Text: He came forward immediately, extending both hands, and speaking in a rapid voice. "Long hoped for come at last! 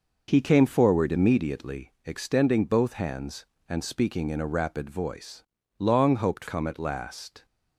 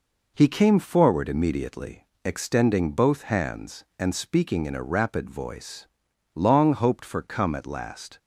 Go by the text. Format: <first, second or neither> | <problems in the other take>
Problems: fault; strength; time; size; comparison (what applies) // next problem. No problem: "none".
second | skips "for"; at 6.4 s